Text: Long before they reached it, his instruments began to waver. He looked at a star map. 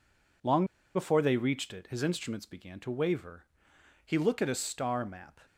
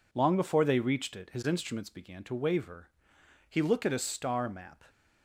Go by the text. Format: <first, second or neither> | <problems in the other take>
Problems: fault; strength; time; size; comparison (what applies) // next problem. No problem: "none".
second | pauses between "Long" and "before"; slight; at 0.6 s; 0.31 s long